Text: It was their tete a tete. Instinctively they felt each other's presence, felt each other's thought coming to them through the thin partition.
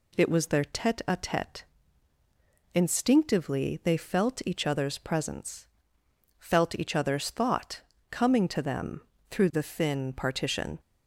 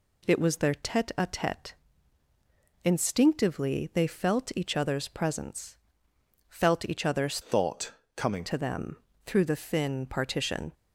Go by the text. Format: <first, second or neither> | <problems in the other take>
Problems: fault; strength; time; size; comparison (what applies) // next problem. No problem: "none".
first | changes voice from "thought" to "coming"; from 7.4 to 8.4 s; 1.0 s long // pauses between "thought" and "coming"; slight; at 7.9 s; 0.24 s long; slight in the first // pauses between "them" and "through"; slight; at 8.9 s; 0.28 s long; slight in the first